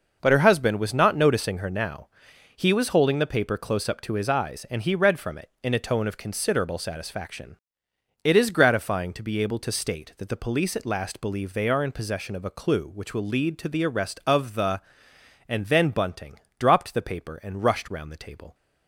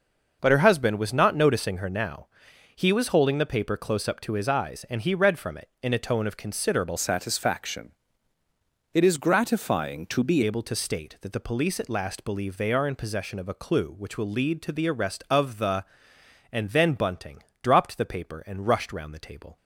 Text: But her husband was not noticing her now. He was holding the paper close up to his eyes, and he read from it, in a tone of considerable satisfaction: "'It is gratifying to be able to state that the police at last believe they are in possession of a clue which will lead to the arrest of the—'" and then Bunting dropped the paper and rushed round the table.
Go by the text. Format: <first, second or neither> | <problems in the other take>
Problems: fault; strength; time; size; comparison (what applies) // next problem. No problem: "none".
first | changes voice from "satisfaction" to "be"; from 6.9 to 10.4 s; 3.5 s long // pauses between "Bunting" and "dropped"; slight; at 17.3 s; 0.24 s long; slight in the first